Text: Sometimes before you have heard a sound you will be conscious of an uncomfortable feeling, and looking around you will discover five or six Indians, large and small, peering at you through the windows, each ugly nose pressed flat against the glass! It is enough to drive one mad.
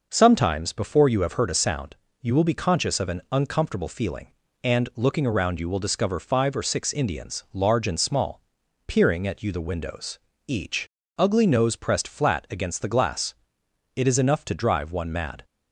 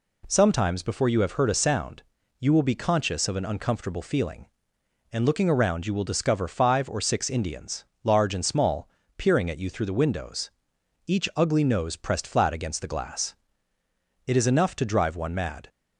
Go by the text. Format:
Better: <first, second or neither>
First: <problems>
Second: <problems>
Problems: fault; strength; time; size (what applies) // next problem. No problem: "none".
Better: second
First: pauses between "sound" and "you"; slight; at 1.9 s; 0.28 s long // skips "through"; at 9.5 s // pauses between "each" and "ugly"; slight; at 10.8 s; 0.30 s long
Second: pauses between "sound" and "you"; at 2.0 s; 0.38 s long